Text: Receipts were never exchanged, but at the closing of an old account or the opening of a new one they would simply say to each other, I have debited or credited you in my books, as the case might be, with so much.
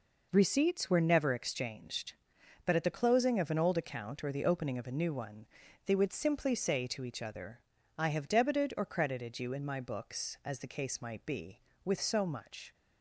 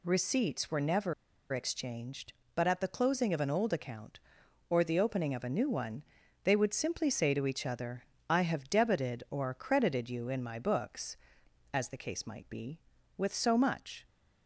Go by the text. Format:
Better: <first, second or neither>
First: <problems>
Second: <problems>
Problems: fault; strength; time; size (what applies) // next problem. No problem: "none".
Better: first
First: pauses between "one" and "they"; at 5.4 s; 0.38 s long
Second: pauses between "never" and "exchanged"; at 1.1 s; 0.39 s long // pauses between "one" and "they"; at 6.0 s; 0.42 s long